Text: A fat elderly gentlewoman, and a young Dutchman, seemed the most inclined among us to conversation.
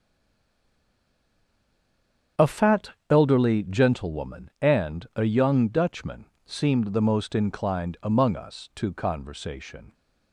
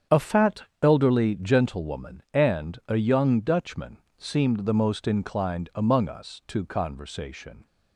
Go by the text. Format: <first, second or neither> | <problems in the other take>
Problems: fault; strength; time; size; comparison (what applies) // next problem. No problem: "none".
second | stays silent before the first word; until 2.3 s; 2.3 s long // starts louder than the rest; strong; until 3.5 s; 7.5 dB; strong in the second // pauses between "fat" and "elderly"; slight; at 2.9 s; 0.18 s long; slight in the second